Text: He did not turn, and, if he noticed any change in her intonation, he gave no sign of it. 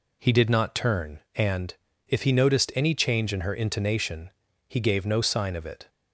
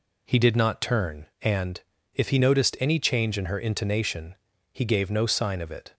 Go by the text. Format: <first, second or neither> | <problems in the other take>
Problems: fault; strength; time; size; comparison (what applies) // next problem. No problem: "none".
neither | none